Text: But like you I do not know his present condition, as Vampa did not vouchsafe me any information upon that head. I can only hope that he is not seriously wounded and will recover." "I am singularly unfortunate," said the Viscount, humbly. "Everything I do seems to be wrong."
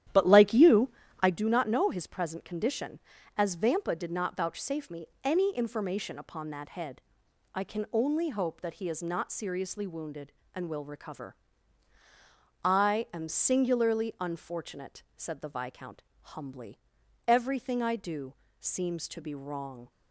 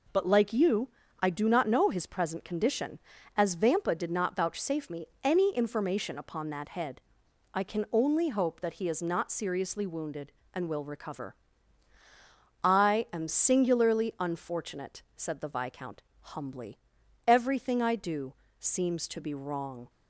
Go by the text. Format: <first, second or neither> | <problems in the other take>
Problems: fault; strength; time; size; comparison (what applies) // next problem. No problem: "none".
second | starts louder than the rest; strong; until 1.4 s; 11 dB // pauses between "you" and "I"; slight; at 0.8 s; 0.30 s long; slight in the second // pauses between "me" and "any"; slight; at 5.0 s; 0.16 s long; slight in the second // pauses between "do" and "seems"; slight; at 18.3 s; 0.24 s long; slight in the second